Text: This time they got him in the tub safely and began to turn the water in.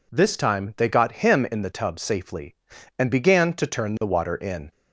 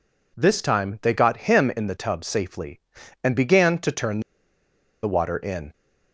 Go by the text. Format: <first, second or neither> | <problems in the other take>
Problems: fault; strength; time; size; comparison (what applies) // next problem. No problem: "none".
first | pauses between "turn" and "the"; noticeable; at 4.1 s; 0.83 s long